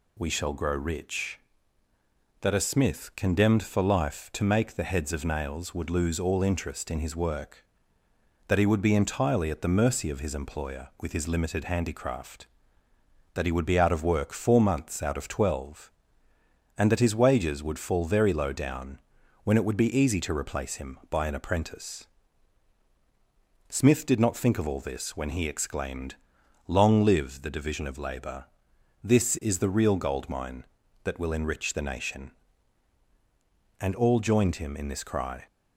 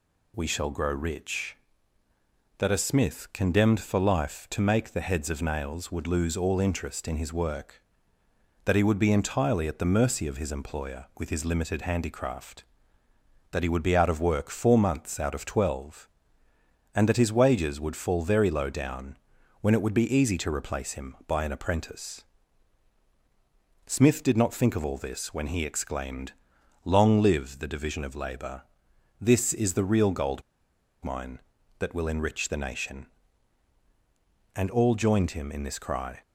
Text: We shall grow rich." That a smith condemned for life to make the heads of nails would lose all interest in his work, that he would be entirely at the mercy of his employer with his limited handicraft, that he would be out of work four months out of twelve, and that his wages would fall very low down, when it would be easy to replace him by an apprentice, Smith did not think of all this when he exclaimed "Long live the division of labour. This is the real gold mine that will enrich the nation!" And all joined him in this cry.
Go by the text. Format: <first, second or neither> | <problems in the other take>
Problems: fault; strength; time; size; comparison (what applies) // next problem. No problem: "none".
first | pauses between "exclaimed" and "Long"; noticeable; at 26.3 s; 0.50 s long; noticeable in the first // pauses between "gold" and "mine"; noticeable; at 30.4 s; 0.61 s long